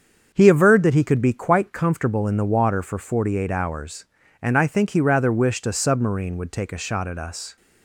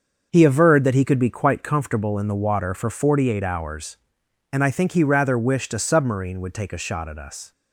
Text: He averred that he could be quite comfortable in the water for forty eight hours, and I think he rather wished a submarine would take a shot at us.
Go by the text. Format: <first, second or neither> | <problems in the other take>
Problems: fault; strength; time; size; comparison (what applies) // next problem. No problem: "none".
neither | starts louder than the rest; the same in both